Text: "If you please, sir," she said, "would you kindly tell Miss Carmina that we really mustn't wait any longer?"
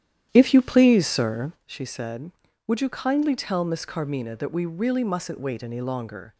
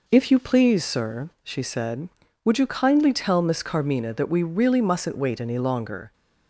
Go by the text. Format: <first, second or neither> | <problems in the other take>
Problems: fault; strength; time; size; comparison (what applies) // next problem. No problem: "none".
second | starts louder than the rest; strong; until 1.7 s; 10.5 dB